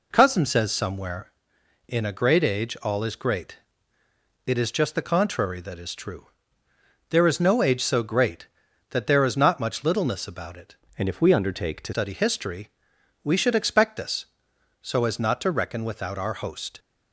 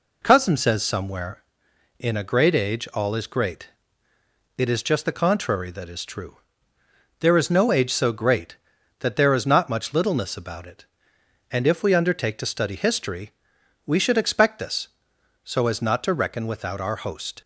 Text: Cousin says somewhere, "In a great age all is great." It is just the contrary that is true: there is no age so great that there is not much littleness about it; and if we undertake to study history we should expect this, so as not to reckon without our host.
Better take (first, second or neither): second